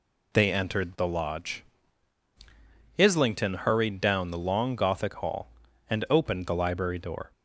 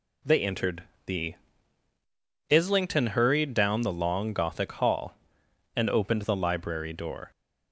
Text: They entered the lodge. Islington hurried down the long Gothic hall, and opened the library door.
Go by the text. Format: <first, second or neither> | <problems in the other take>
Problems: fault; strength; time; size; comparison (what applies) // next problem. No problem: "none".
first | pauses between "entered" and "the"; slight; at 0.8 s; 0.22 s long // skips "lodge"; at 1.9 s